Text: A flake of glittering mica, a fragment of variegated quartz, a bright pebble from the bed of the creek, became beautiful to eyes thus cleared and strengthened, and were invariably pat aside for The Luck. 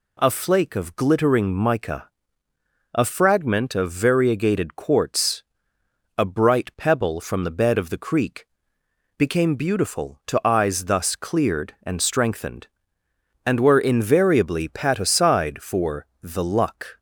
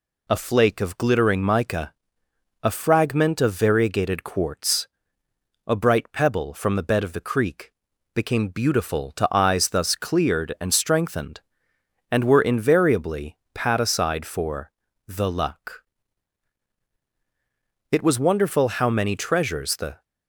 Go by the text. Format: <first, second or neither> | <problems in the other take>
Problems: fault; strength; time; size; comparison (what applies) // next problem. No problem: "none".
first | pauses between "invariably" and "pat"; slight; at 13.3 s; 0.16 s long // pauses between "for" and "The"; slight; at 14.7 s; 0.36 s long; slight in the first // goes on to say "It was wonderful how many treasures the"; strong; from 17.9 s on; 2.1 s long